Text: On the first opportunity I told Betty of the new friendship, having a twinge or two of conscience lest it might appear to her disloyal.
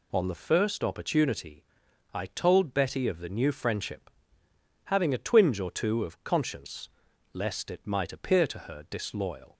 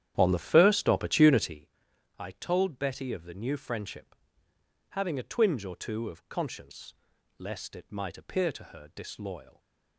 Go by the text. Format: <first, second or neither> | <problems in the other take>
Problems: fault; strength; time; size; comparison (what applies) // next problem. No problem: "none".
first | starts louder than the rest; strong; until 1.7 s; 10.5 dB // pauses between "opportunity" and "I"; noticeable; at 1.6 s; 0.50 s long; noticeable in the first // pauses between "conscience" and "lest"; at 6.9 s; 0.44 s long; also in the first